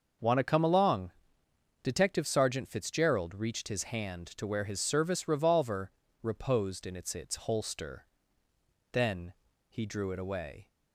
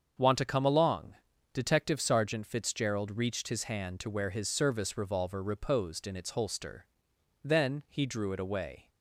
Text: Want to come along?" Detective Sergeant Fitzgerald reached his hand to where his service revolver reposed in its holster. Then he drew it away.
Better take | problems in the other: second | starts louder than the rest; noticeable; until 1.9 s; 6 dB; also in the second // pauses between "revolver" and "reposed"; slight; at 5.9 s; 0.32 s long // says "its" twice; at 7.1 s // pauses between "Then" and "he"; slight; at 9.3 s; 0.34 s long

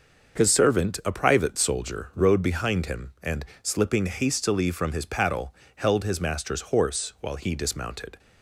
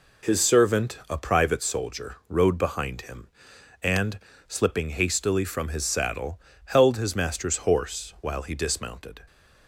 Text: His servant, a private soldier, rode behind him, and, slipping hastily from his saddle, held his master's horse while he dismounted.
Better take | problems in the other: second | starts louder than the rest; until 1.4 s; 6 dB // says "paddle" for "saddle"; at 5.0 s

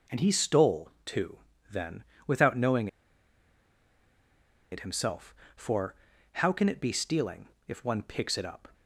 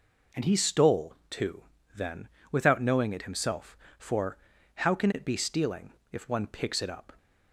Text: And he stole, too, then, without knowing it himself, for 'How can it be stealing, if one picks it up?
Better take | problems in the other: second | pauses between "knowing" and "it"; strong; at 2.8 s; 1.8 s long // pauses between "for" and "How"; at 5.9 s; 0.38 s long; also in the second

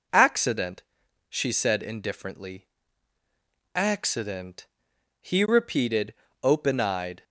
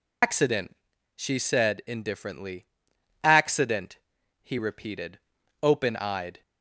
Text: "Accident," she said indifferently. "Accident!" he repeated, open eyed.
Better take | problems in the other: first | loses the start of "Accident"; at 0.2 s; 125 ms

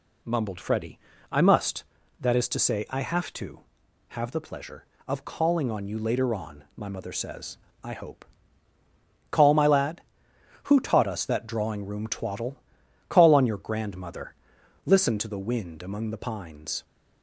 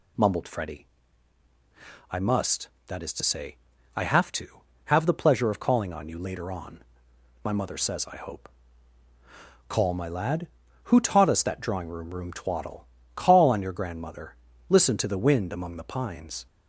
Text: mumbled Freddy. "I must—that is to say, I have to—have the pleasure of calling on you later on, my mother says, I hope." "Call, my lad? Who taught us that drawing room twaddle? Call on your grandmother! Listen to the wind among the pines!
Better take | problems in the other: first | says "room" twice; at 12.1 s

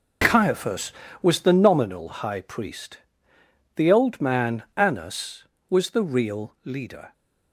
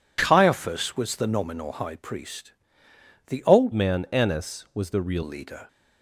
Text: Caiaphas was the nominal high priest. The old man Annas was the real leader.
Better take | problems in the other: first | changes voice from "man" to "real"; from 3.7 to 5.2 s; 1.5 s long

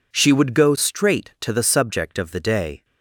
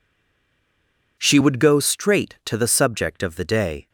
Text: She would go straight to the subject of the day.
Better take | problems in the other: first | stays silent before the first word; noticeable; until 1.1 s; 1.1 s long

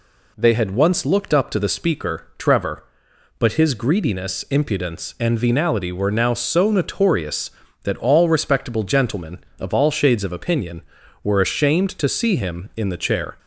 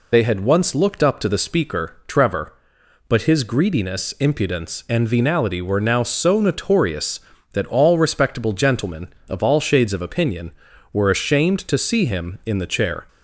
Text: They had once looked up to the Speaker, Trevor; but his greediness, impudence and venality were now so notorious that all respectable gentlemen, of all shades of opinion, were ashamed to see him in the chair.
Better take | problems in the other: first | loses the start of "They"; at 0.1 s; 70 ms

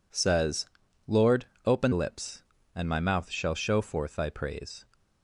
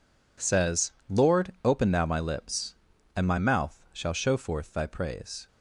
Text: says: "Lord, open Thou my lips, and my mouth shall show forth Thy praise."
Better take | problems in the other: second | skips "Thou my"; at 1.9 s

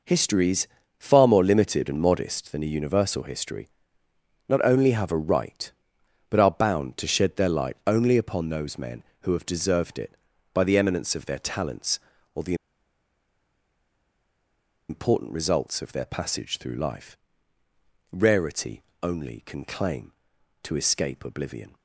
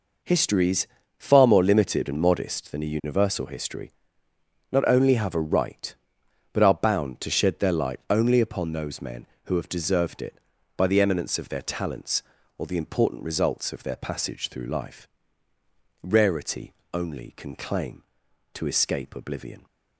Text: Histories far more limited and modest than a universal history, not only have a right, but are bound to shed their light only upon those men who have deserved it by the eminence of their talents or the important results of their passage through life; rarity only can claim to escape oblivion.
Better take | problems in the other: second | pauses between "Histories" and "far"; slight; at 0.6 s; 0.32 s long; slight in the second // pauses between "the" and "important"; strong; at 12.5 s; 2.3 s long // pauses between "rarity" and "only"; slight; at 18.8 s; 0.18 s long; slight in the second

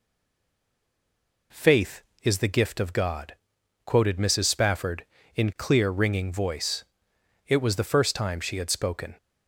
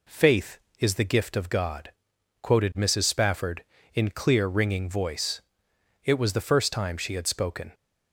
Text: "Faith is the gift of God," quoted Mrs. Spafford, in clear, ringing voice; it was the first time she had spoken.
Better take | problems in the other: second | stays silent before the first word; noticeable; until 1.5 s; 1.5 s long

